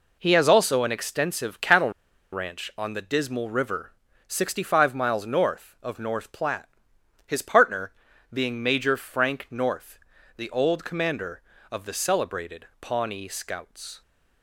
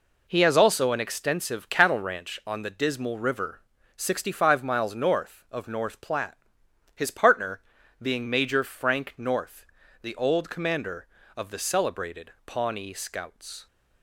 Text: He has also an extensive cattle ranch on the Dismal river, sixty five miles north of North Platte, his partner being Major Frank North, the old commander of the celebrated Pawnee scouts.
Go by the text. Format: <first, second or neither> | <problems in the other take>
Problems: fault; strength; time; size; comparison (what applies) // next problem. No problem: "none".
second | pauses between "cattle" and "ranch"; at 1.9 s; 0.41 s long // pauses between "partner" and "being"; at 7.9 s; 0.40 s long; also in the second // pauses between "celebrated" and "Pawnee"; slight; at 12.6 s; 0.16 s long; slight in the second